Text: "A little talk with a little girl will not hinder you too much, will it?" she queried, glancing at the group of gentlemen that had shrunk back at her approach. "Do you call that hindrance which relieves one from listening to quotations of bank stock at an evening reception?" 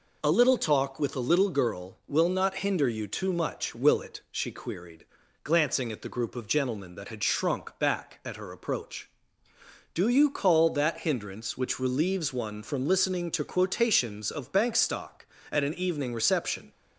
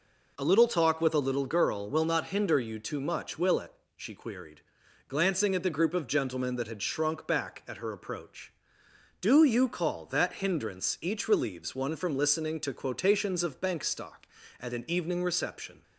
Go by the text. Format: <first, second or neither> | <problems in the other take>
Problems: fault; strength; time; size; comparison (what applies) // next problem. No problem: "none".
first | says "each" for "which"; at 11.0 s